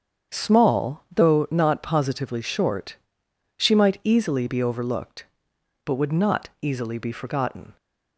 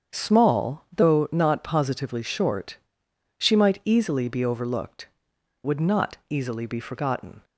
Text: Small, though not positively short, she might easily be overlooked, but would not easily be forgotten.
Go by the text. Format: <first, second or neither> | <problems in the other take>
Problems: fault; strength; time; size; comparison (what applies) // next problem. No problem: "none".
first | starts louder than the rest; strong; until 1.2 s; 7.5 dB; strong in the first // skips "but"; at 5.3 s